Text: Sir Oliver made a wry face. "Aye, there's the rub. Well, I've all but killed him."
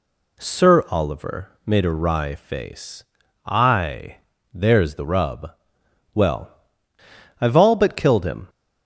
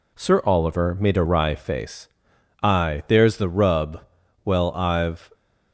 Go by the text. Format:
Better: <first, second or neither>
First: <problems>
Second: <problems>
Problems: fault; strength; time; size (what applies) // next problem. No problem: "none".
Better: first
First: none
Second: stops before "all but killed him"; at 5.3 s